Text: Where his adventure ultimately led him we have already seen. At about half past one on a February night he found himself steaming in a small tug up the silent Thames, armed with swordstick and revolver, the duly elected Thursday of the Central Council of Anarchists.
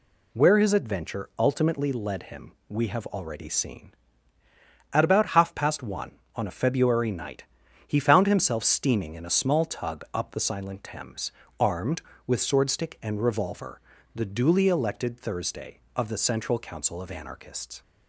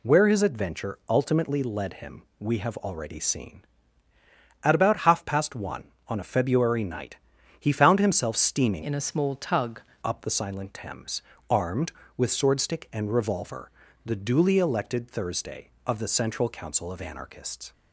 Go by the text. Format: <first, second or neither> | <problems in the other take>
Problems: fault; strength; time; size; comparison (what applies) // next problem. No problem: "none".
first | pauses between "him" and "we"; slight; at 2.2 s; 0.16 s long; slight in the first // pauses between "night" and "he"; at 7.1 s; 0.42 s long; also in the first // changes voice from "in" to "tug"; from 8.8 to 9.8 s; 1.0 s long